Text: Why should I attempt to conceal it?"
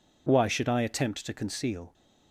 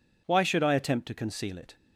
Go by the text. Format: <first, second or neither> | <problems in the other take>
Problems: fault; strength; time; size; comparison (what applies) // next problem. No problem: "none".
second | stops before "it"; at 1.9 s